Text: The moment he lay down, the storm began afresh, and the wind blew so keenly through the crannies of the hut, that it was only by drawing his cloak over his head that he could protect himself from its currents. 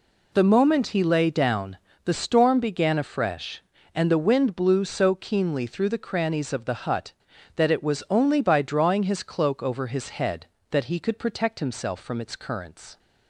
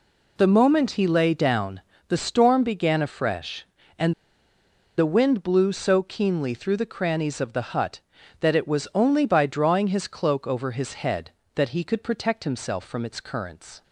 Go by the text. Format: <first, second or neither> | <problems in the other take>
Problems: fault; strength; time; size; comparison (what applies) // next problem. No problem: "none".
first | pauses between "and" and "the"; noticeable; at 4.1 s; 0.84 s long